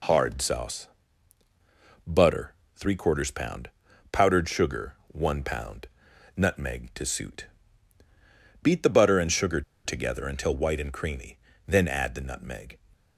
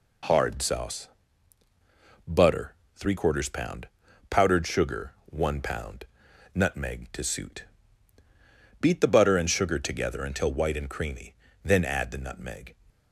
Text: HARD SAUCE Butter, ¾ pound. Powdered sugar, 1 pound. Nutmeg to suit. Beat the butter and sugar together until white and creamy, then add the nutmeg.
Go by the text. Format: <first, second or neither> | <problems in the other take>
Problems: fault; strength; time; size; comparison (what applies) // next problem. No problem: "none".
second | pauses between "SAUCE" and "Butter"; at 0.8 s; 1.1 s long; also in the second // pauses between "sugar" and "together"; slight; at 9.6 s; 0.24 s long